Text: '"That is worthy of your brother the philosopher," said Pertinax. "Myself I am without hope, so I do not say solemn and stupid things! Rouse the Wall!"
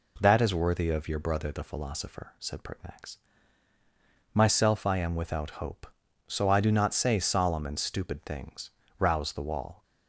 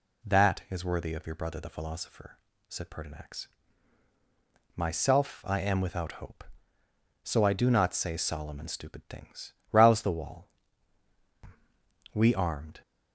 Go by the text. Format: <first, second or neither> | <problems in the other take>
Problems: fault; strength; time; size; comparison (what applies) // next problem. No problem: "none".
first | goes on to say "We armed"; noticeable; from 12.1 s on; 0.68 s long